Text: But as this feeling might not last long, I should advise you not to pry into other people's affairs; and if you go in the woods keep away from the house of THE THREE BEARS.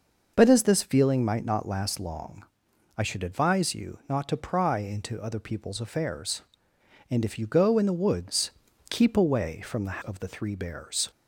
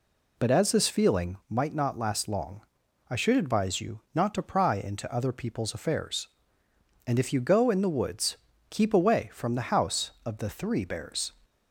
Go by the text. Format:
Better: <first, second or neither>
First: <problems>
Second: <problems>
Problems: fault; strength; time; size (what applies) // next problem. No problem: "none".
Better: second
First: pauses between "woods" and "keep"; at 8.4 s; 0.40 s long // skips "house"; at 10.0 s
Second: pauses between "woods" and "keep"; slight; at 8.3 s; 0.34 s long